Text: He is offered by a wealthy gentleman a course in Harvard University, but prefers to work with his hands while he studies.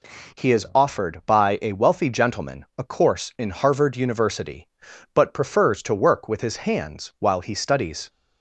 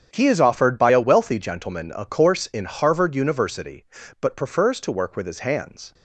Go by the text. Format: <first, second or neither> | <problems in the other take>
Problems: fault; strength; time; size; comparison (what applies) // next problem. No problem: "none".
first | starts louder than the rest; strong; until 1.1 s; 8.5 dB // stops before "while he studies"; at 5.9 s